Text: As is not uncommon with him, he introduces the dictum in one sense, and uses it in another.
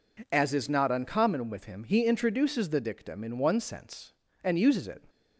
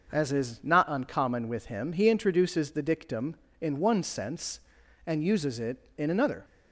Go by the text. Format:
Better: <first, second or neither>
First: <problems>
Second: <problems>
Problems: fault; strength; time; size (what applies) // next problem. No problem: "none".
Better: second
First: stops before "in another"; at 5.0 s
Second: none